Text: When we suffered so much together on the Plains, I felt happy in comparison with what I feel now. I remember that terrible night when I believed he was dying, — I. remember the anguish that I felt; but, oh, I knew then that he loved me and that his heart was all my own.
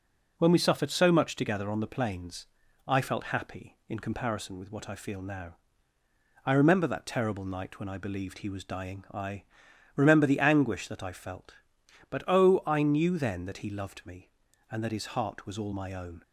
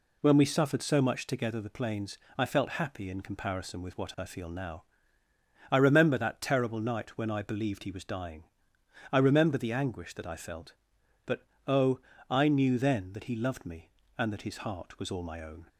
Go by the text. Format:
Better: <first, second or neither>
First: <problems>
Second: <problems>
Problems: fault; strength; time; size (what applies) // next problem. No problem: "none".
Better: first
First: none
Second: skips "on"; at 1.6 s